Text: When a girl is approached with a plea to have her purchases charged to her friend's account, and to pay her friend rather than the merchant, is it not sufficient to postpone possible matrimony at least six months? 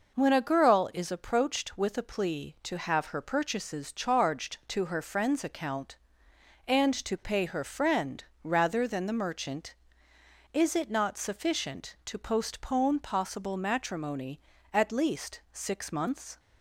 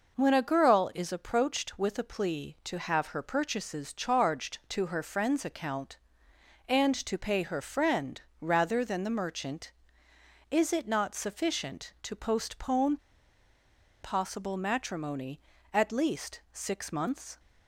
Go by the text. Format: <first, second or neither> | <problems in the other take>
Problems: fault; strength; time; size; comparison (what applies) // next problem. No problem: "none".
first | pauses between "friend" and "rather"; slight; at 8.2 s; 0.20 s long; slight in the first // pauses between "postpone" and "possible"; at 12.9 s; 1.0 s long